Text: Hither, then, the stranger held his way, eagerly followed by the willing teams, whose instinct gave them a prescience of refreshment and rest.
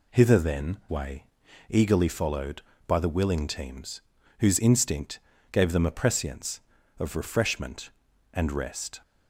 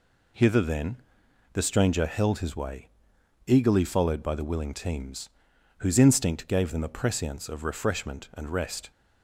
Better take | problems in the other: second | skips "the stranger held his"; at 0.8 s // pauses between "instinct" and "gave"; slight; at 5.1 s; 0.32 s long

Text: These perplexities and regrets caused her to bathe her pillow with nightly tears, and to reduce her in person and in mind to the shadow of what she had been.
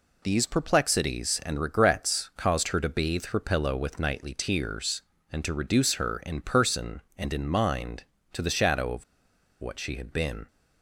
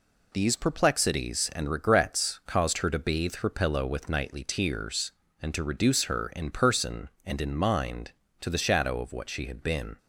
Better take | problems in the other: second | pauses between "of" and "what"; noticeable; at 9.0 s; 0.56 s long

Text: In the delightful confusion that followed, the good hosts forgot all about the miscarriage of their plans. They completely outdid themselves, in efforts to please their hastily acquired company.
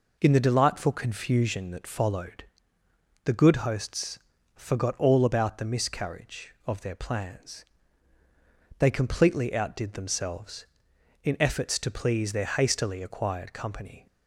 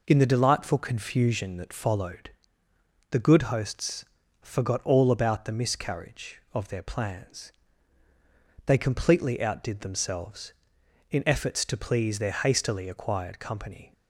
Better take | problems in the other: neither | pauses between "hosts" and "forgot"; the same in both

